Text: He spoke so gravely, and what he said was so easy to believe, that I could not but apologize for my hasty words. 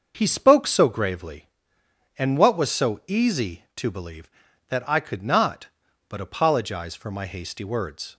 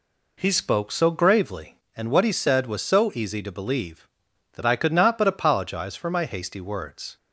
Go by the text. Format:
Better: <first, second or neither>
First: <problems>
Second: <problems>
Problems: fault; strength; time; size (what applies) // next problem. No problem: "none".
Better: second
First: starts louder than the rest; until 1.1 s; 6 dB // skips "he said"; at 2.5 s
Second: none